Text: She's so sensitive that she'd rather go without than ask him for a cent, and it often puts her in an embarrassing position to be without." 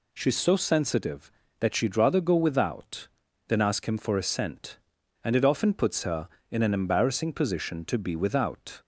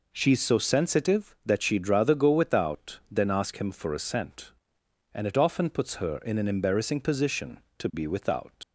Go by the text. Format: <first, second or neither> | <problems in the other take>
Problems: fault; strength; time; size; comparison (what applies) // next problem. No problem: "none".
first | leaves "without" unfinished; at 8.6 s; 75 ms